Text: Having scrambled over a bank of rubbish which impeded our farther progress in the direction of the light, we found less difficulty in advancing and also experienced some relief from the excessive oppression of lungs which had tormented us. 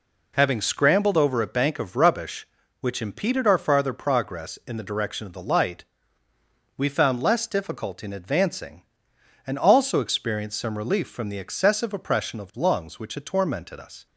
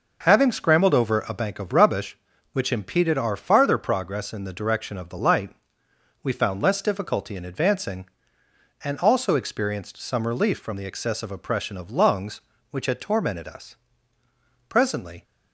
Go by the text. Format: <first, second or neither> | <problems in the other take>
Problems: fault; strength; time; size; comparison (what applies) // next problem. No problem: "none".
first | goes on to say "Presently"; from 14.6 s on; 0.54 s long